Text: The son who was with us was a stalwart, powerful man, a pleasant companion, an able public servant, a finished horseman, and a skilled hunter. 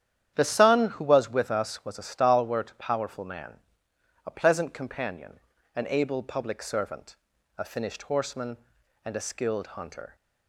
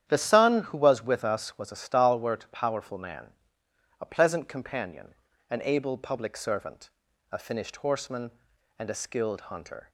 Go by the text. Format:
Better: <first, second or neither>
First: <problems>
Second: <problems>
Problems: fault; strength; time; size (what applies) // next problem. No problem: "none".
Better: neither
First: starts louder than the rest; strong; until 1.3 s; 10 dB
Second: starts louder than the rest; strong; until 1.0 s; 10 dB